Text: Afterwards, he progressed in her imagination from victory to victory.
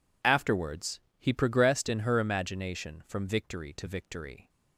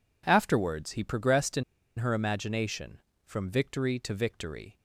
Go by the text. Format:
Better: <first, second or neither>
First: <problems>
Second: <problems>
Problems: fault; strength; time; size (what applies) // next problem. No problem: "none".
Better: first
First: none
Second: pauses between "in" and "her"; slight; at 1.6 s; 0.35 s long